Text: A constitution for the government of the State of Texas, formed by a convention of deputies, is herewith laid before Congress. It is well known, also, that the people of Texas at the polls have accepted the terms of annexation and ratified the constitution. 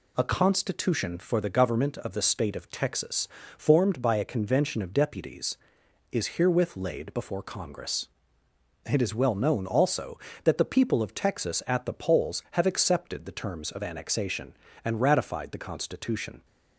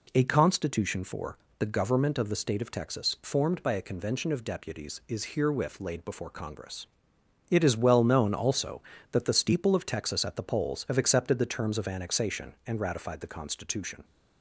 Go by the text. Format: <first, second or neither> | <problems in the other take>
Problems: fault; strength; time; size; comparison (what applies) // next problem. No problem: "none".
first | pauses between "for" and "the"; slight; at 1.3 s; 0.22 s long // says "steeple" for "people"; at 9.3 s